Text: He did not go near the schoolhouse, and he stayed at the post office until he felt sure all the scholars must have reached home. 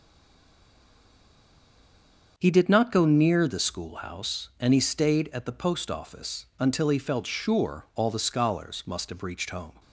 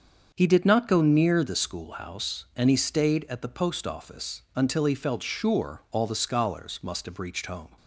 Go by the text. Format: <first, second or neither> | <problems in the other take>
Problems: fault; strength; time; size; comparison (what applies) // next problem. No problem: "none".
second | stays silent before the first word; until 2.3 s; 2.3 s long // starts louder than the rest; until 3.3 s; 7 dB; also in the second